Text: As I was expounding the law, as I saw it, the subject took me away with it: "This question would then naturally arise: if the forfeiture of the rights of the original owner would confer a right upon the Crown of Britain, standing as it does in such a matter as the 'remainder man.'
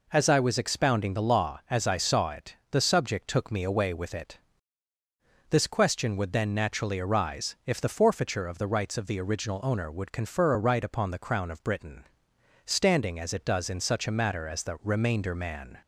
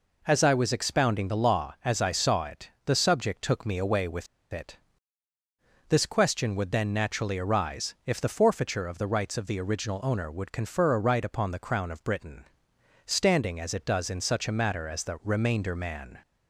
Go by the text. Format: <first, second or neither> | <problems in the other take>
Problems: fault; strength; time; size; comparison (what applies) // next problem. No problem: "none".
first | pauses between "with" and "it"; slight; at 4.2 s; 0.26 s long